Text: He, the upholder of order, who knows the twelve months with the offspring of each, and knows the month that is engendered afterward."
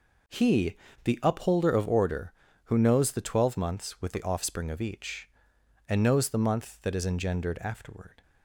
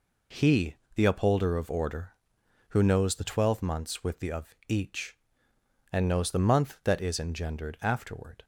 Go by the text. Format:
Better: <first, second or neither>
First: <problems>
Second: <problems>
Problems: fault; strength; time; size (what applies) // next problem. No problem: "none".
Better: first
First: none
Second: skips "offspring"; at 4.3 s